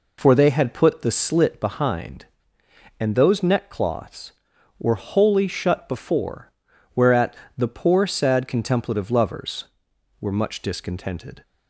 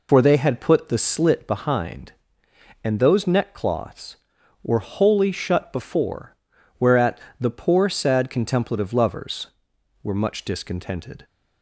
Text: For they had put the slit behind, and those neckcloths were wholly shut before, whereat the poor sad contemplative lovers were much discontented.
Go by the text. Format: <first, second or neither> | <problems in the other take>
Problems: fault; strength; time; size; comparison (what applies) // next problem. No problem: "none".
first | loses the start of "For"; at 0.0 s; 40 ms // pauses between "whereat" and "the"; slight; at 7.1 s; 0.22 s long; slight in the first